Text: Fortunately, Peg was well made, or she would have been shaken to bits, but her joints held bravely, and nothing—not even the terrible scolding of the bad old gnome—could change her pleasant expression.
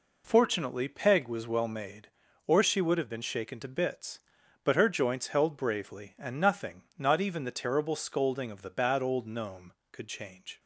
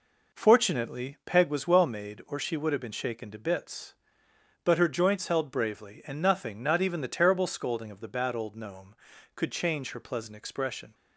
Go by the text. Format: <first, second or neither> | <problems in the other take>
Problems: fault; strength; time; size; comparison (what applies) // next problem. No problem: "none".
second | stops before "her pleasant expression"; at 10.5 s